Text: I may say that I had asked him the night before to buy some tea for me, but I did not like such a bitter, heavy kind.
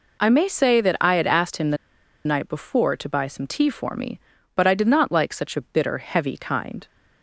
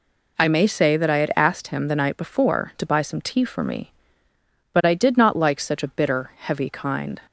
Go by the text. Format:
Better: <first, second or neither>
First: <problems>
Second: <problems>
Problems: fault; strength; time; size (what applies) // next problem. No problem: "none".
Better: second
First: pauses between "the" and "night"; noticeable; at 1.7 s; 0.49 s long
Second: none